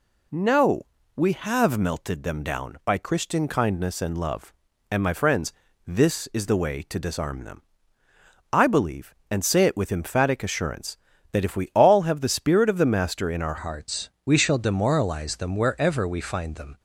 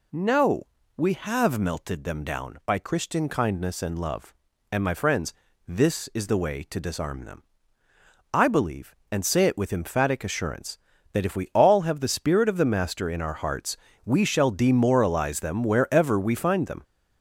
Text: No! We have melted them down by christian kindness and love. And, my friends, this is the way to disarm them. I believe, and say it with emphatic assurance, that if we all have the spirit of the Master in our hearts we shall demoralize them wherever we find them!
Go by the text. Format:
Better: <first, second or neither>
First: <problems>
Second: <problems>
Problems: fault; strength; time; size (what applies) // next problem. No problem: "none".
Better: second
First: changes voice at "hearts"; from 13.5 s on; 3.2 s long // pauses between "hearts" and "we"; slight; at 14.0 s; 0.16 s long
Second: pauses between "hearts" and "we"; slight; at 13.7 s; 0.26 s long